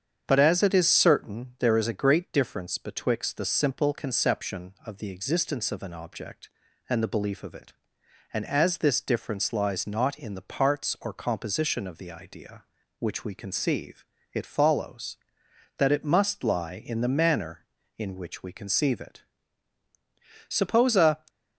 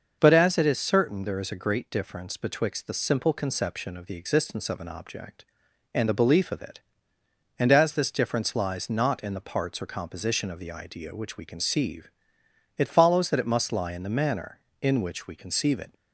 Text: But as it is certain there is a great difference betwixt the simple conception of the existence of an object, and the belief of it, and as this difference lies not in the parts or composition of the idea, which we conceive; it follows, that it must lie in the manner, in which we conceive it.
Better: second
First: starts louder than the rest; strong; until 1.2 s; 8 dB // goes on to say "Suppose a"; noticeable; from 20.4 s on; 0.70 s long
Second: starts louder than the rest; noticeable; until 1.2 s; 6 dB

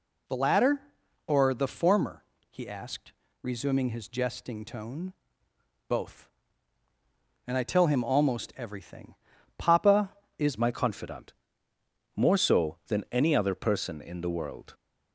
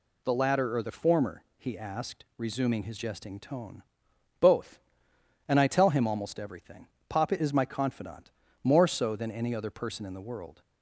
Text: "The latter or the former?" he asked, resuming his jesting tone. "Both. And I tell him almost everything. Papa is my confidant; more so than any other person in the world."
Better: second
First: changes voice at "my"; from 10.5 s on; 4.2 s long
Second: none

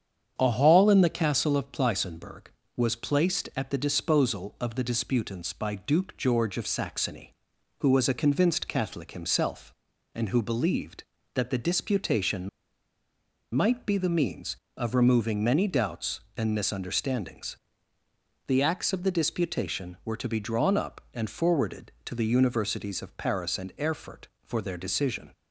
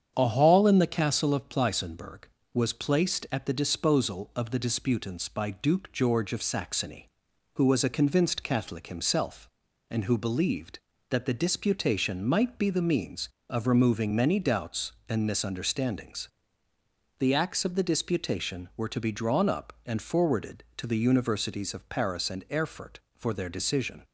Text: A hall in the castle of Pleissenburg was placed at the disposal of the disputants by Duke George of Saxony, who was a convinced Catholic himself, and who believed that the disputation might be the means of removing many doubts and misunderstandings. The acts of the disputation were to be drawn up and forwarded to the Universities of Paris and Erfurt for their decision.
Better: second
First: starts louder than the rest; strong; until 1.3 s; 8 dB // pauses between "disputation" and "might"; at 12.4 s; 1.0 s long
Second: starts louder than the rest; strong; until 1.1 s; 8 dB

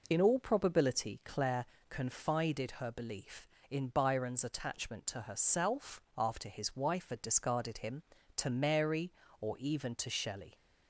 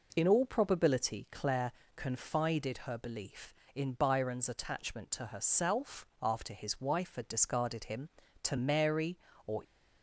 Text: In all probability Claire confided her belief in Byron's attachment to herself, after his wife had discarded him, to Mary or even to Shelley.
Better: first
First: pauses between "Claire" and "confided"; slight; at 1.6 s; 0.24 s long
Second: pauses between "Claire" and "confided"; slight; at 1.7 s; 0.24 s long // stops before "even to Shelley"; at 9.6 s

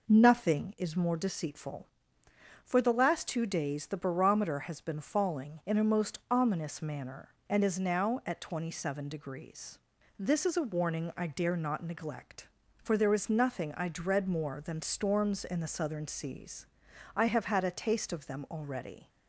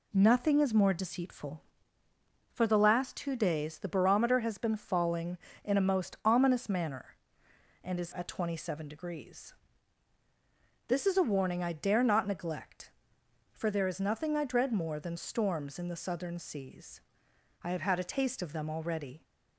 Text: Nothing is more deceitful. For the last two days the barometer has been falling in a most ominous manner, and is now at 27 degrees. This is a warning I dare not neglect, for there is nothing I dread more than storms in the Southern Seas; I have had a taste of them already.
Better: first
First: none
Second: skips "now"; at 8.1 s

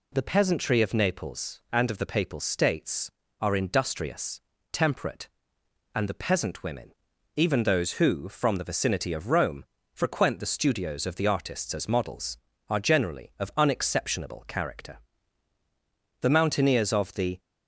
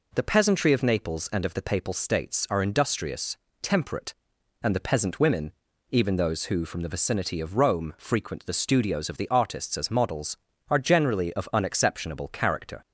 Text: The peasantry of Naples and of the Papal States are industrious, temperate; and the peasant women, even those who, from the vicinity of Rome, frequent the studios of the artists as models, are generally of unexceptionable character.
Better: second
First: goes on to say "The mountaineers of the"; noticeable; from 16.2 s on; 1.1 s long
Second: none

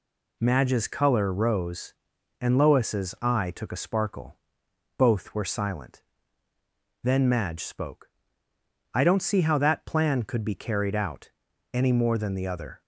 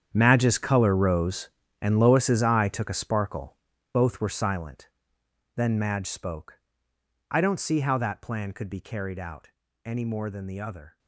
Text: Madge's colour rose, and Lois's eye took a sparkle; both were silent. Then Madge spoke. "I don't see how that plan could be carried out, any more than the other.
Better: first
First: none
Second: gets quieter; strong; throughout; 15 dB

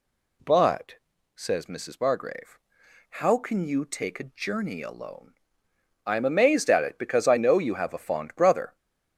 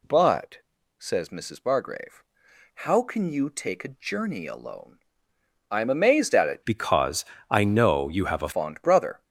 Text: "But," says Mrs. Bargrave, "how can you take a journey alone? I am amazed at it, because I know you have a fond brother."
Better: first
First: none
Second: changes voice from "because" to "a"; from 6.6 to 8.5 s; 1.9 s long // pauses between "because" and "I"; slight; at 7.2 s; 0.24 s long

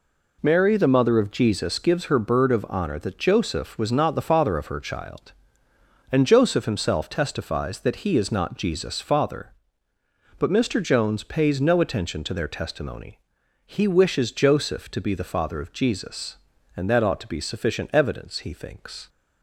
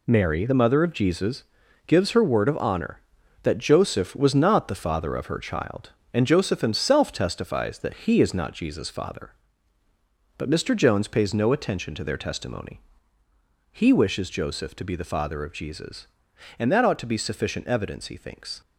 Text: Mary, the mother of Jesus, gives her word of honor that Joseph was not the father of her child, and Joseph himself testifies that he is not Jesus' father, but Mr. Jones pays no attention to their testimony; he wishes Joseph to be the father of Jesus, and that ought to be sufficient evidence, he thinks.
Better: second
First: says "bird" for "word"; at 2.1 s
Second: none

